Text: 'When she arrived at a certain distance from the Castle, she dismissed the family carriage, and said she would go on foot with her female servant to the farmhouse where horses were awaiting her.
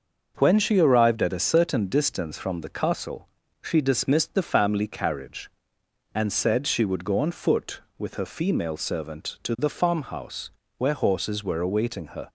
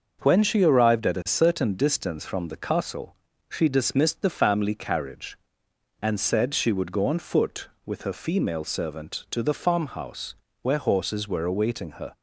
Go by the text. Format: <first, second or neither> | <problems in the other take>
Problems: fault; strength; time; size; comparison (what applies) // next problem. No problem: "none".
neither | starts louder than the rest; noticeable; the same in both // pauses between "farmhouse" and "where"; slight; the same in both